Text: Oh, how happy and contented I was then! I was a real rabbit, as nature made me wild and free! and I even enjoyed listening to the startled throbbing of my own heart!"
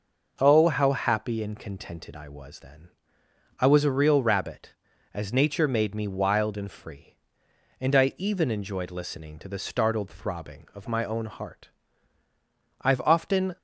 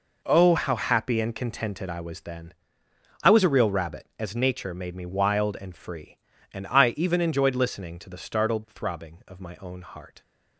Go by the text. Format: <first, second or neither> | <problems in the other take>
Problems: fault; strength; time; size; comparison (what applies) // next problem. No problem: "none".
second | goes on to say "I've often"; noticeable; from 12.8 s on; 0.76 s long